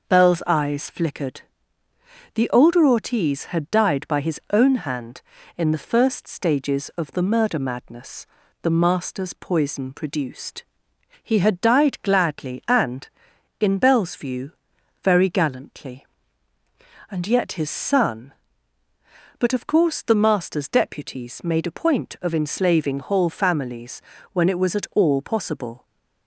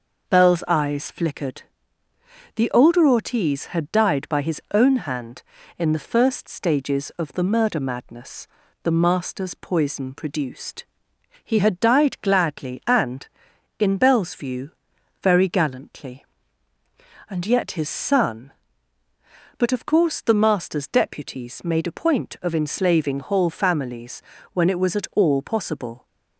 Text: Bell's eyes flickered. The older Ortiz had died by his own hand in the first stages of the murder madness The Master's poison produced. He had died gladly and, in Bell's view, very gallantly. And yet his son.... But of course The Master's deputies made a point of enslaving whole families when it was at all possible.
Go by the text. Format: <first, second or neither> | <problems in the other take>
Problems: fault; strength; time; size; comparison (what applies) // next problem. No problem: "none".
neither | pauses between "madness" and "The"; slight; the same in both // pauses between "families" and "when"; slight; the same in both